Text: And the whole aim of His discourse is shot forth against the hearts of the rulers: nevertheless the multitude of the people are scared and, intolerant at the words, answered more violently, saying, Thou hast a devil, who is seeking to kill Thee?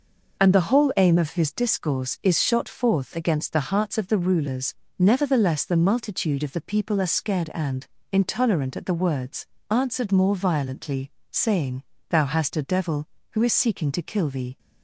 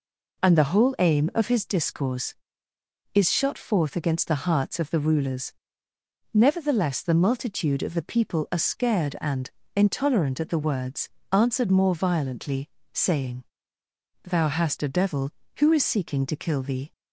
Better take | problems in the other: neither | none

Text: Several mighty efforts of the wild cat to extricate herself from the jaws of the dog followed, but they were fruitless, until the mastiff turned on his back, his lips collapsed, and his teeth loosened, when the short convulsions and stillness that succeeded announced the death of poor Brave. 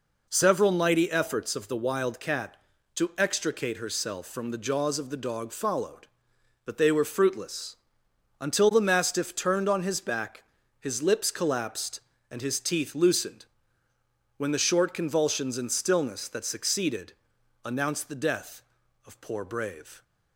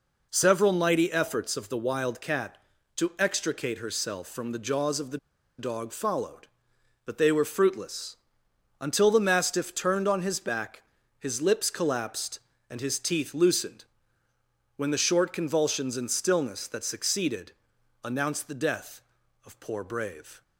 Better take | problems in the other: first | pauses between "the" and "dog"; at 5.1 s; 0.41 s long // pauses between "succeeded" and "announced"; noticeable; at 17.5 s; 0.52 s long; noticeable in the first

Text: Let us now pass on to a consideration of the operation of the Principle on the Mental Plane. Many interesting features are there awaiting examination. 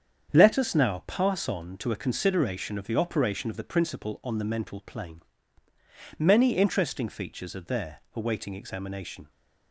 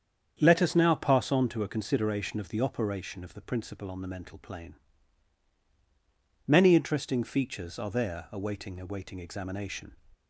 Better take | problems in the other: first | starts louder than the rest; strong; until 1.4 s; 8 dB; strong in the first // says "awaiting" twice; at 8.7 s

